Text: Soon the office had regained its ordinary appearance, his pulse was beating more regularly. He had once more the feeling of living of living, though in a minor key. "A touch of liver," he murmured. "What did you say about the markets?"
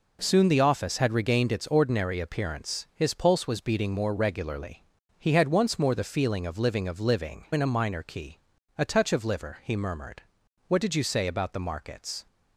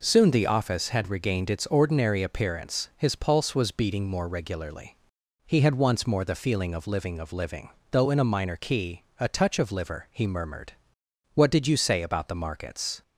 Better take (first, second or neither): second